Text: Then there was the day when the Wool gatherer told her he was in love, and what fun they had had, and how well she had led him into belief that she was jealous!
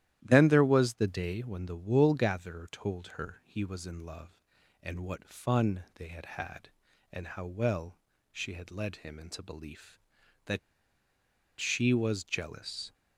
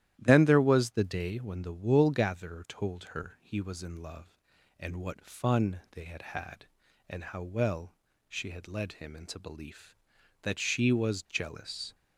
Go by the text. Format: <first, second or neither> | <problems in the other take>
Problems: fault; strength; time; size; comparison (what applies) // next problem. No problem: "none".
second | starts louder than the rest; strong; until 1.2 s; 12.5 dB; strong in the second // pauses between "well" and "she"; slight; at 7.9 s; 0.32 s long; slight in the second // pauses between "that" and "she"; at 10.5 s; 1.0 s long